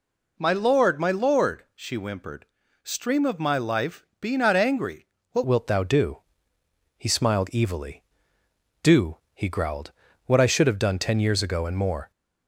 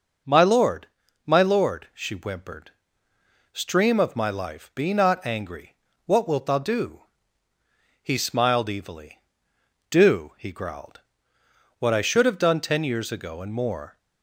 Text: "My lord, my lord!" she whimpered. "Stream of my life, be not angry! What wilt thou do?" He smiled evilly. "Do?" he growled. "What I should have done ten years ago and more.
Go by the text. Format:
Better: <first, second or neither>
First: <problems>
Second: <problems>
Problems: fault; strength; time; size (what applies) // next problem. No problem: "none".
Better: second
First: changes voice at "wilt"; from 5.4 s on; 6.7 s long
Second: none